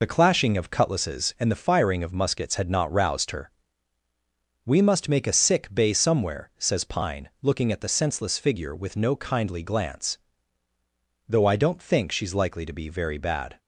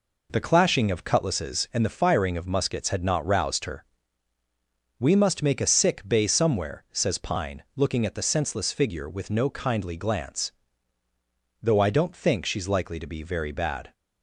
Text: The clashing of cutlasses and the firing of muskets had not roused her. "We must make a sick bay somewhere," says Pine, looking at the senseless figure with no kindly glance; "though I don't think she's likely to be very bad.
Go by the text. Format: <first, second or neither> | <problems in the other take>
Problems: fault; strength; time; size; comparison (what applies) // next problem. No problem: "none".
second | loses the start of "The"; at 0.0 s; 50 ms